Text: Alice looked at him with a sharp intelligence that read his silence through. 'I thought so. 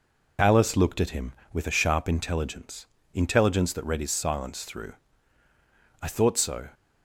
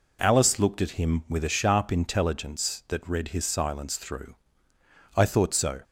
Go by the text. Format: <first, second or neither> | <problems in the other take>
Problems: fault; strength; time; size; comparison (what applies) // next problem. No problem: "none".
second | says "intelligence" twice; at 3.1 s